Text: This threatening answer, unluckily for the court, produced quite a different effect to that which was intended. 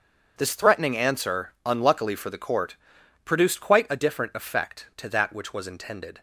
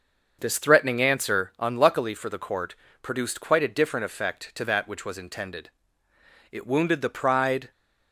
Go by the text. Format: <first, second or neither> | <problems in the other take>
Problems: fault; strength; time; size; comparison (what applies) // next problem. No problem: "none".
first | starts louder than the rest; noticeable; until 1.4 s; 6 dB; also in the first // goes on to say "It wounded the pride"; noticeable; from 6.5 s on; 1.2 s long